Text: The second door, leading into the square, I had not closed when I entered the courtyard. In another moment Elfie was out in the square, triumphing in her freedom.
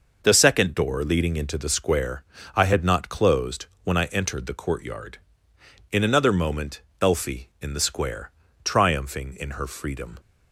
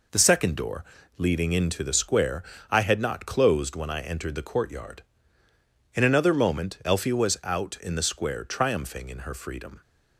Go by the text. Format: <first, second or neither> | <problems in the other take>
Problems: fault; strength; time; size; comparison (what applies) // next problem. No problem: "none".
second | pauses between "closed" and "when"; slight; at 3.6 s; 0.18 s long // pauses between "moment" and "Elfie"; slight; at 6.8 s; 0.18 s long // skips "was out"; at 7.5 s